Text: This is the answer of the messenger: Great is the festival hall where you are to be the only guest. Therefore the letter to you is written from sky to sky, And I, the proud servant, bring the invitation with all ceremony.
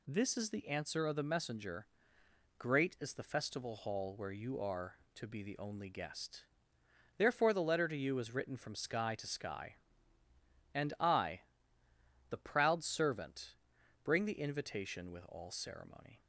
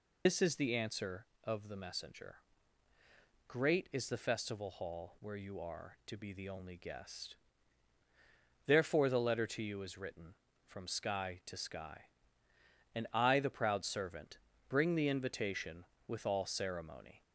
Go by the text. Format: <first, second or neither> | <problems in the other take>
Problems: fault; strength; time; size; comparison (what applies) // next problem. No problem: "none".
first | loses the start of "This"; at 0.2 s; 95 ms